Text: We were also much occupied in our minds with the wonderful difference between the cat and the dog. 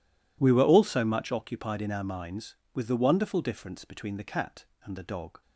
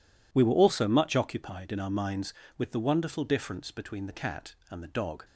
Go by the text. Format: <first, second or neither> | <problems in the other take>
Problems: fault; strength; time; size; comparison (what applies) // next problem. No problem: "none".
neither | none